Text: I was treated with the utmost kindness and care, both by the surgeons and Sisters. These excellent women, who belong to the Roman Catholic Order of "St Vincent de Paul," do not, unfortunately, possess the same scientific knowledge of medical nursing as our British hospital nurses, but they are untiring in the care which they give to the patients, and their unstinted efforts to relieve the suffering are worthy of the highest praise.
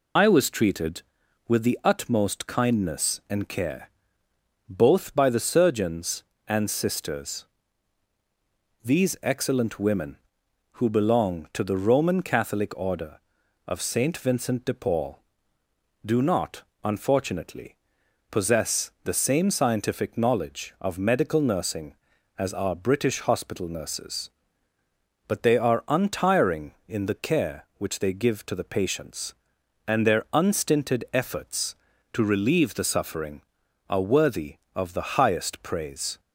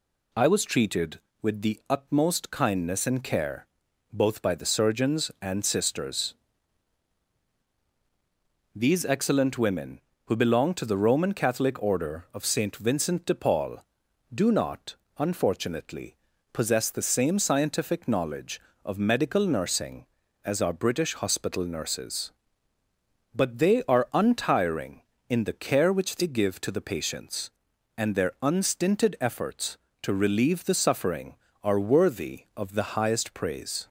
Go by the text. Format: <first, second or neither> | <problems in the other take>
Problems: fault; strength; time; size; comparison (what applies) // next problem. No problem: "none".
second | loses the start of "I"; at 0.1 s; 50 ms